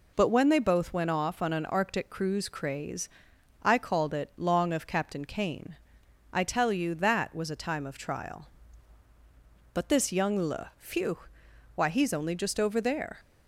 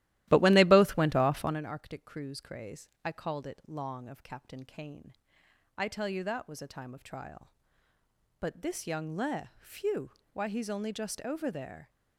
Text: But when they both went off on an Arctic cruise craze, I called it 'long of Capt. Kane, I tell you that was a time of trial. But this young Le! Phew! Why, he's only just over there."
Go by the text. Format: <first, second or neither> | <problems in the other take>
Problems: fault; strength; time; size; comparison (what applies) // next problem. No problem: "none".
first | starts louder than the rest; strong; until 1.6 s; 15.5 dB